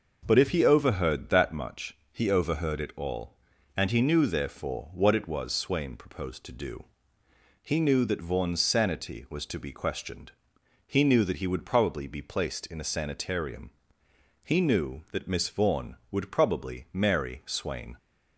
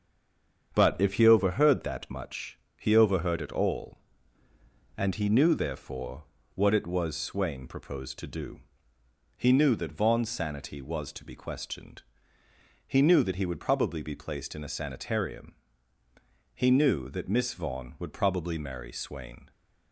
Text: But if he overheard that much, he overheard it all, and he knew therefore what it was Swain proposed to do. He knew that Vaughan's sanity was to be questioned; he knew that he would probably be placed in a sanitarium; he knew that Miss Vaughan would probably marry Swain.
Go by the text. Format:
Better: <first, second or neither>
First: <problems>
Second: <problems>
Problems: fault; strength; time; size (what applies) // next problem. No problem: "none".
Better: first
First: none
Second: stays silent before the first word; slight; until 0.7 s; 0.7 s long // starts louder than the rest; strong; until 1.7 s; 7.5 dB // pauses between "therefore" and "what"; slight; at 6.2 s; 0.32 s long